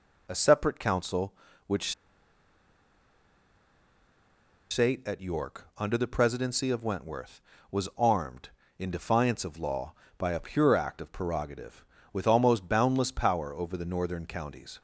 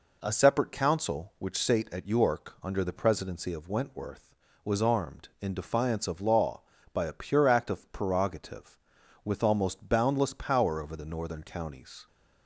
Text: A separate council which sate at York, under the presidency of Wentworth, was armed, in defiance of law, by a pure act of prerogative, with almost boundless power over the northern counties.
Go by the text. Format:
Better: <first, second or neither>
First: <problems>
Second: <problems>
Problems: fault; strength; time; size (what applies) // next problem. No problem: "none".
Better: second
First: pauses between "which" and "sate"; strong; at 1.9 s; 2.7 s long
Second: none